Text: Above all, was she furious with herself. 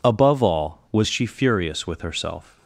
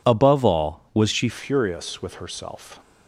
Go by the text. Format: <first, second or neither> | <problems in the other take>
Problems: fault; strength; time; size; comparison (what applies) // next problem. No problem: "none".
first | changes voice at "furious"; from 1.2 s on; 1.5 s long